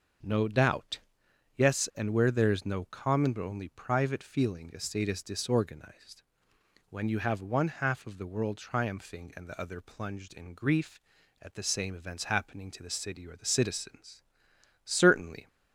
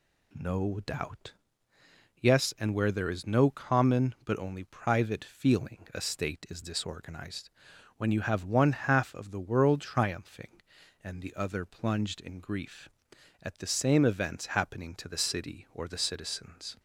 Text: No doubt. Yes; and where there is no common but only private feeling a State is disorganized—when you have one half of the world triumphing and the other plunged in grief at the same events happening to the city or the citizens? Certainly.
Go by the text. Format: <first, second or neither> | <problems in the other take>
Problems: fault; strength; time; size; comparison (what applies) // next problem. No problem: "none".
first | stops before "Certainly"; at 16.7 s